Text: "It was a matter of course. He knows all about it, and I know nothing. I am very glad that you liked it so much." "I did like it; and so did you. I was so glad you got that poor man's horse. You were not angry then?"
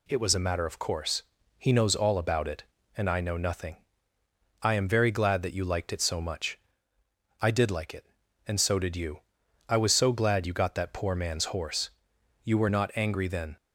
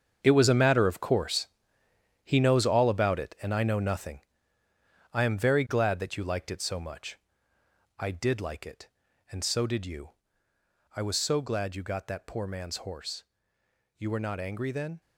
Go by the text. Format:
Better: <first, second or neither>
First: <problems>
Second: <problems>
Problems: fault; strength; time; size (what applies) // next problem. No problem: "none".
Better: first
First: none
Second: gets quieter; strong; throughout; 12 dB